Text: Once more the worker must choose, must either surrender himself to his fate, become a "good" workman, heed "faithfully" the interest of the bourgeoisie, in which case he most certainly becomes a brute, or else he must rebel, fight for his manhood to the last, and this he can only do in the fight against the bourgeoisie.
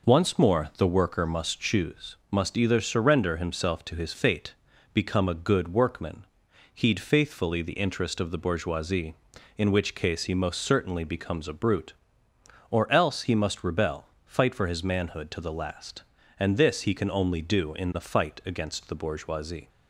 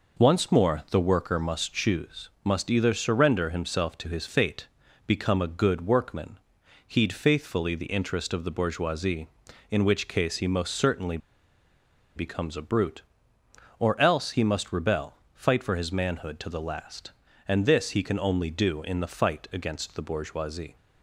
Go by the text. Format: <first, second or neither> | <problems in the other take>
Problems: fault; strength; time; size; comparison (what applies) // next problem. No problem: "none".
first | pauses between "certainly" and "becomes"; at 11.1 s; 0.98 s long